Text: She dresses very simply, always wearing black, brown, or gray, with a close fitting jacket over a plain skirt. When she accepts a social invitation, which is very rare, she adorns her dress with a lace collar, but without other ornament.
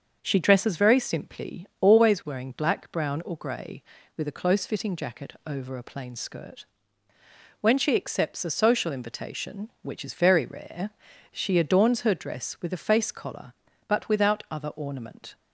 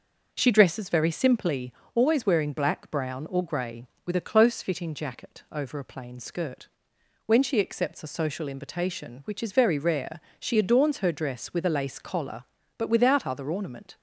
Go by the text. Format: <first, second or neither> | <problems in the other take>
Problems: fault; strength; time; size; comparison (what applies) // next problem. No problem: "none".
second | starts louder than the rest; until 1.2 s; 6.5 dB; noticeable in the second // says "face" for "lace"; at 12.8 s